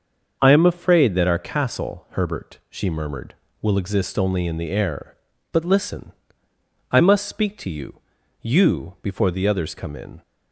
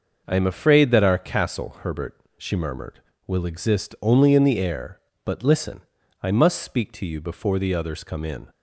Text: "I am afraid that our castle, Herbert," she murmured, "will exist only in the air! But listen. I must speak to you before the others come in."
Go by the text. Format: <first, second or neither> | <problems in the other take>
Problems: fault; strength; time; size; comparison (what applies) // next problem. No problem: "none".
second | starts louder than the rest; until 1.4 s; 6.5 dB // says "you" twice; at 8.4 s